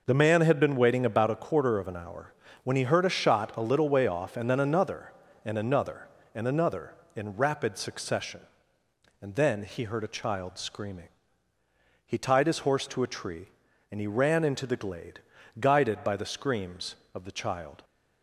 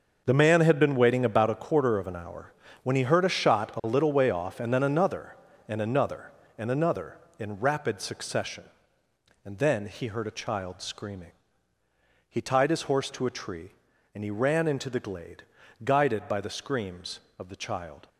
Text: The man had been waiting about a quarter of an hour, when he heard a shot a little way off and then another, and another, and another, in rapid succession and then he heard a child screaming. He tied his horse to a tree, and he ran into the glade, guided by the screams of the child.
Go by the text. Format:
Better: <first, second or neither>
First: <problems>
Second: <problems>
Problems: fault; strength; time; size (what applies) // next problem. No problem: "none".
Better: first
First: none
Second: gets quieter; strong; throughout; 11 dB